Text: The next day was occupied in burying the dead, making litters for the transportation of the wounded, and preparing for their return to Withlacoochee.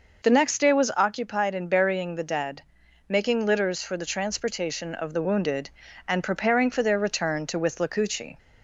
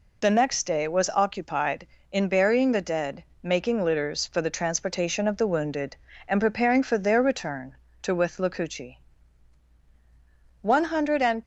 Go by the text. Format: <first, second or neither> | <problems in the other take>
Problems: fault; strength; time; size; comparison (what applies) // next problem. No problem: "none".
first | goes on to say "One hundred and"; noticeable; from 10.6 s on; 0.80 s long